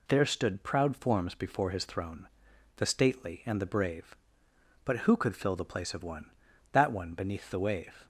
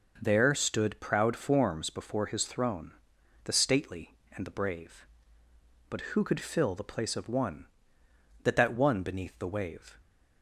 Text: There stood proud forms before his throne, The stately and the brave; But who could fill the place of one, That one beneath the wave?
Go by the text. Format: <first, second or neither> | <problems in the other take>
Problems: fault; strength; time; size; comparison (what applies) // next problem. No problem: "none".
first | says "That" twice; at 8.5 s